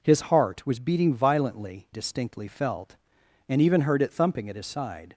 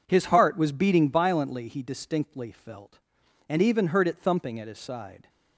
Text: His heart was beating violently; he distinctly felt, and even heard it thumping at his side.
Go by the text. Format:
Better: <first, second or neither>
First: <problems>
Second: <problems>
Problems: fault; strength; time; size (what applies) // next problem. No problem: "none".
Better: second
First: skips "he"; at 1.8 s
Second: none